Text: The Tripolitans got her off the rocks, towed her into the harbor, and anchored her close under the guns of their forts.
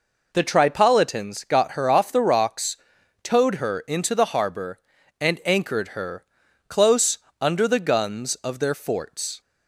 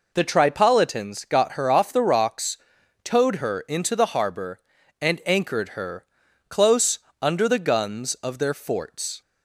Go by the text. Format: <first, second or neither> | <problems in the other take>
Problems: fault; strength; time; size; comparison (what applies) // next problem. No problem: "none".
neither | pauses between "her" and "close"; the same in both // pauses between "close" and "under"; slight; the same in both